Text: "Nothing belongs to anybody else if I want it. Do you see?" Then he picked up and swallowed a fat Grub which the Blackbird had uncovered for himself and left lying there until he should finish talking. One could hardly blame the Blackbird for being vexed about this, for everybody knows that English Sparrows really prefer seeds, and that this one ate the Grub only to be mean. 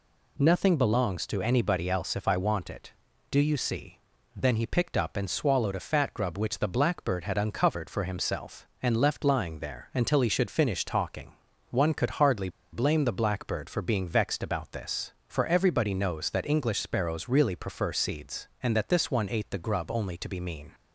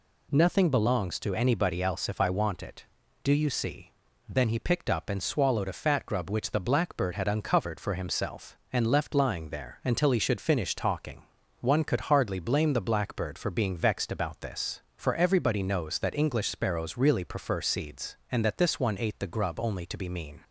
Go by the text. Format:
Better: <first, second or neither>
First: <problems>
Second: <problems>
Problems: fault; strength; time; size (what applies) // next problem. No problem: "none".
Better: second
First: pauses between "hardly" and "blame"; slight; at 12.4 s; 0.23 s long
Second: none